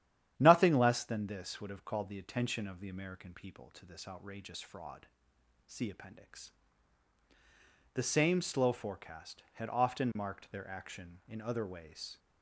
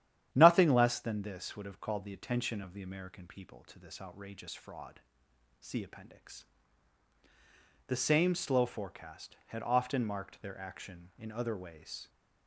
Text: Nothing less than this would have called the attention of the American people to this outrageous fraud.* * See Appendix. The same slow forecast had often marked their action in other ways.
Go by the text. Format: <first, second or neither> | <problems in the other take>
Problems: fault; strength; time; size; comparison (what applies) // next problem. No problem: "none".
neither | starts louder than the rest; strong; the same in both